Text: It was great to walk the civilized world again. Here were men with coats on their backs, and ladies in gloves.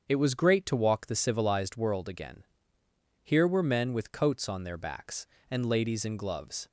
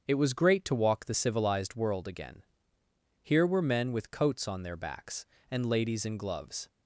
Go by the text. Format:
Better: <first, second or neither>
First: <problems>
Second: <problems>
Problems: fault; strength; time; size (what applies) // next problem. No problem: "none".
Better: neither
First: starts louder than the rest; strong; until 1.0 s; 7.5 dB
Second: starts louder than the rest; strong; until 1.0 s; 7.5 dB